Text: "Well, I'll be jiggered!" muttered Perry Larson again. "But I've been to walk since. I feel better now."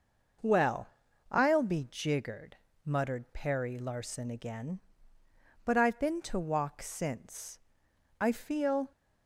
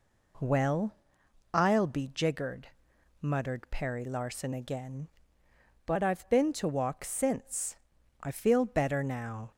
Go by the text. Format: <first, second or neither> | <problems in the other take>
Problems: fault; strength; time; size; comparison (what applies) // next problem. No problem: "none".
second | stops before "better now"; at 8.9 s